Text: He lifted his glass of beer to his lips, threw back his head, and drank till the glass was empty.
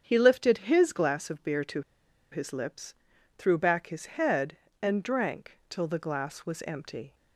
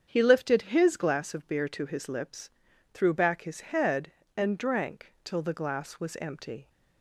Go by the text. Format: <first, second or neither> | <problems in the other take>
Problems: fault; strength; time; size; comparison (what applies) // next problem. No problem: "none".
second | starts louder than the rest; strong; until 1.0 s; 7.5 dB; strong in the second // pauses between "to" and "his"; noticeable; at 1.8 s; 0.51 s long